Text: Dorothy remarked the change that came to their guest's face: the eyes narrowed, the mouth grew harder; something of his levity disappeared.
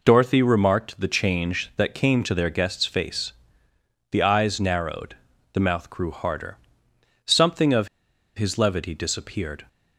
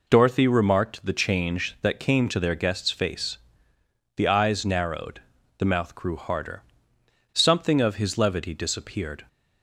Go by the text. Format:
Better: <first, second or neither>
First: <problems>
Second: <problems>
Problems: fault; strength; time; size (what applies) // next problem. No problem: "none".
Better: second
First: pauses between "of" and "his"; noticeable; at 7.8 s; 0.49 s long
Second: none